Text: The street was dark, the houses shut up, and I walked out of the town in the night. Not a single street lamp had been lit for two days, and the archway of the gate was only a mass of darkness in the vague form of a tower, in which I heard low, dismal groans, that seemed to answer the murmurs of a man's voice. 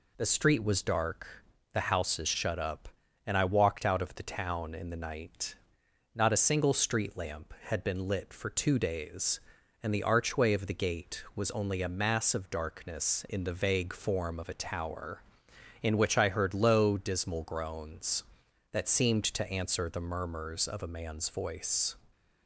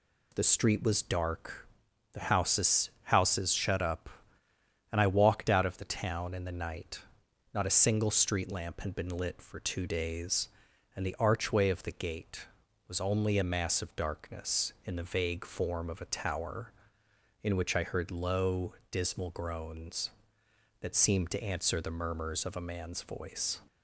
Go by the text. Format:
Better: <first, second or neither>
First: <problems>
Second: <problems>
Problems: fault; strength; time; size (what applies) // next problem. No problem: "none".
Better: first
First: none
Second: says "houses" twice; at 3.0 s